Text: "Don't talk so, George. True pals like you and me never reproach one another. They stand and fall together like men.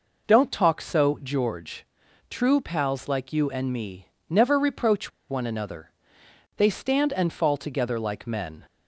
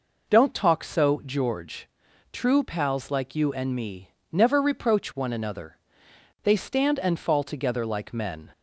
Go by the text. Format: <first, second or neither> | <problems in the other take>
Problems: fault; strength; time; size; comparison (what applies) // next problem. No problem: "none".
second | pauses between "me" and "never"; slight; at 4.0 s; 0.18 s long; slight in the second // pauses between "reproach" and "one"; slight; at 5.1 s; 0.19 s long